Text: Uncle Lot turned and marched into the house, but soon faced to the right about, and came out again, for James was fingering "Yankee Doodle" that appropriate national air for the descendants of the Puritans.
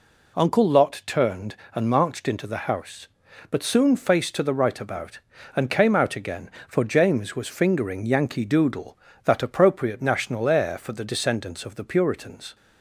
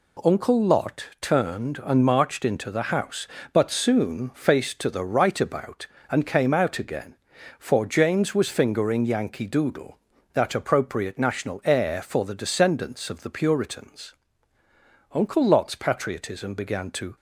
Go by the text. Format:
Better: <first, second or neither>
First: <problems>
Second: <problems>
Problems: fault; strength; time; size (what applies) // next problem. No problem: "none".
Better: first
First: none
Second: goes on to say "Uncle Lot's patriotism began to"; strong; from 15.1 s on; 2.0 s long